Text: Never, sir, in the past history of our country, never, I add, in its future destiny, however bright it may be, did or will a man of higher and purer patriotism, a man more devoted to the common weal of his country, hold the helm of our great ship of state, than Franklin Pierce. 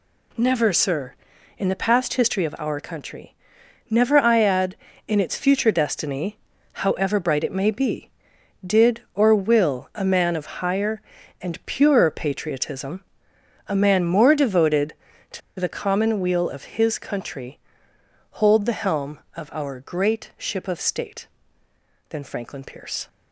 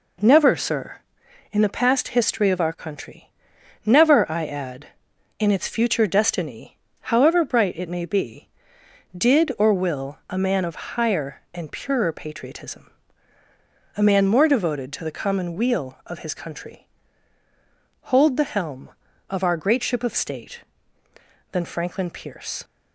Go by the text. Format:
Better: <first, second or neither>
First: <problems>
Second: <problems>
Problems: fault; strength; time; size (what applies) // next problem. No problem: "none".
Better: second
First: pauses between "to" and "the"; slight; at 15.4 s; 0.19 s long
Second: none